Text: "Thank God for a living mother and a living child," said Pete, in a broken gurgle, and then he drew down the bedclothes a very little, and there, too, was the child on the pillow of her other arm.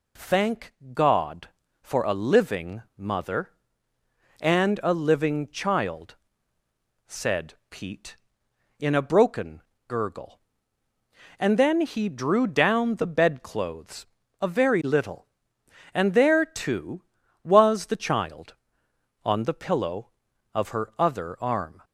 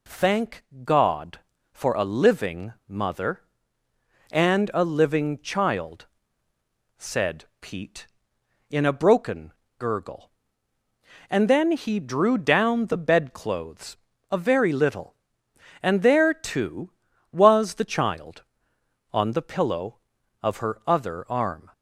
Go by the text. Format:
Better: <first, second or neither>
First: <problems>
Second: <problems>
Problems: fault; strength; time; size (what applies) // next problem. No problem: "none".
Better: neither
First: pauses between "Thank" and "God"; slight; at 0.7 s; 0.22 s long // pauses between "living" and "mother"; slight; at 2.8 s; 0.16 s long // pauses between "said" and "Pete"; slight; at 7.5 s; 0.16 s long // pauses between "broken" and "gurgle"; slight; at 9.6 s; 0.28 s long // pauses between "bedclothes" and "a"; slight; at 14.0 s; 0.34 s long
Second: pauses between "Thank" and "God"; slight; at 0.6 s; 0.22 s long // pauses between "living" and "mother"; slight; at 2.7 s; 0.16 s long // pauses between "said" and "Pete"; slight; at 7.4 s; 0.16 s long // pauses between "broken" and "gurgle"; slight; at 9.5 s; 0.28 s long // pauses between "bedclothes" and "a"; slight; at 13.9 s; 0.33 s long